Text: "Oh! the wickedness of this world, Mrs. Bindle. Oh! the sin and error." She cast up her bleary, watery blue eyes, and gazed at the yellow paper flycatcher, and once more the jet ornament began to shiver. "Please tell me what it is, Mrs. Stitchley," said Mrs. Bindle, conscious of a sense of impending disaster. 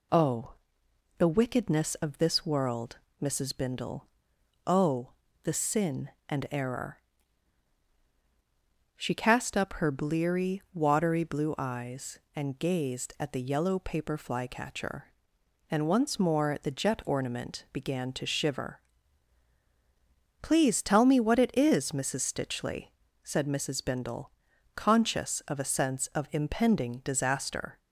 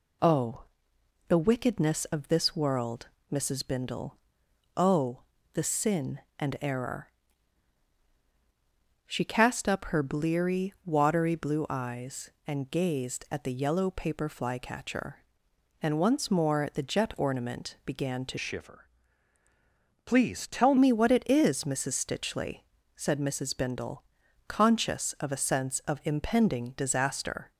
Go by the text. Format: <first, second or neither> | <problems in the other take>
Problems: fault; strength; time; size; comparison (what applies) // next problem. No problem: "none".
first | changes voice from "shiver" to "tell"; from 18.3 to 20.7 s; 2.4 s long